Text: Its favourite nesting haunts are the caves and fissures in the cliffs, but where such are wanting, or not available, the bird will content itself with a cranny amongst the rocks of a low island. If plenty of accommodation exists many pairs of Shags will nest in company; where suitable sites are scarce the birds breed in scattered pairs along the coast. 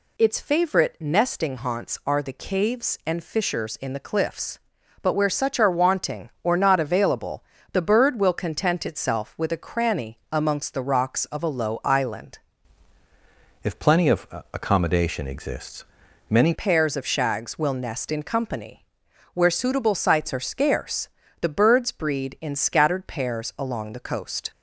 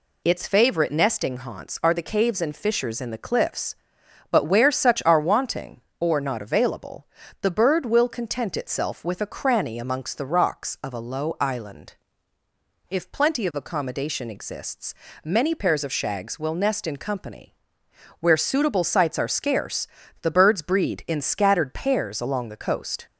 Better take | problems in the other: second | changes voice from "If" to "many"; from 13.6 to 16.5 s; 2.9 s long // pauses between "of" and "accommodation"; slight; at 14.2 s; 0.26 s long // pauses between "exists" and "many"; at 15.8 s; 0.44 s long; slight in the second // pauses between "scarce" and "the"; slight; at 21.0 s; 0.32 s long; slight in the second

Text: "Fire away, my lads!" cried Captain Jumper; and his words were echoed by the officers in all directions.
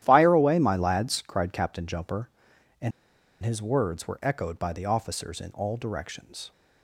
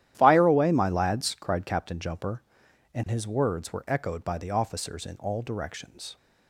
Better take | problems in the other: second | starts louder than the rest; strong; until 1.0 s; 11.5 dB; strong in the second // pauses between "and" and "his"; noticeable; at 2.9 s; 0.51 s long

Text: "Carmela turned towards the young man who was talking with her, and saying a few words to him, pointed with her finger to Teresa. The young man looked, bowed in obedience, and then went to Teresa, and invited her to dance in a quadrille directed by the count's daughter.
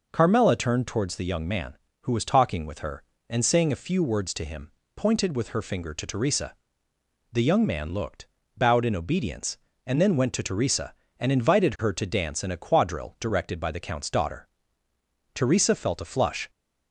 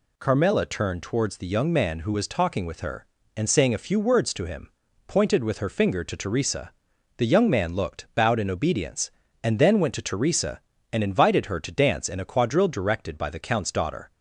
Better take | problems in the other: second | goes on to say "Teresa felt a flush"; noticeable; from 15.3 s on; 1.1 s long

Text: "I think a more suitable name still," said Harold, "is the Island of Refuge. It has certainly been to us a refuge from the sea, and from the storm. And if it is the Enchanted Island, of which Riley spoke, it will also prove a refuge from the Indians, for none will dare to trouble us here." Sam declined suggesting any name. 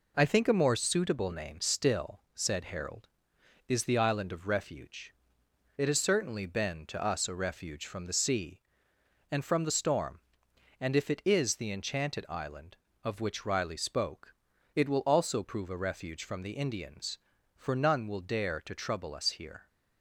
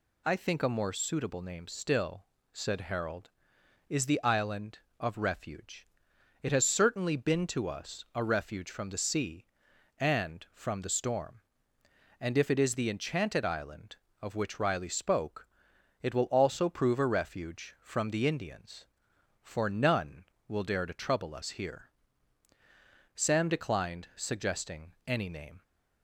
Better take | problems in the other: second | stops before "Sam declined suggesting any name"; at 19.6 s

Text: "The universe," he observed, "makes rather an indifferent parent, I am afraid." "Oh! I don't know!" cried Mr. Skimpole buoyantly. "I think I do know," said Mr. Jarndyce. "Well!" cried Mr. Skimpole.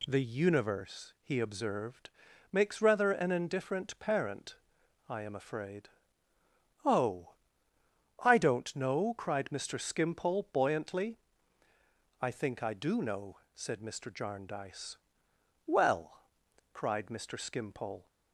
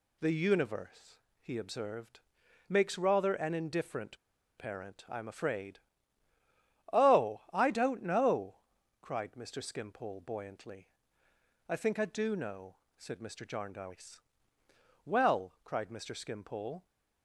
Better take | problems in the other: first | pauses between "indifferent" and "parent"; at 4.1 s; 0.41 s long

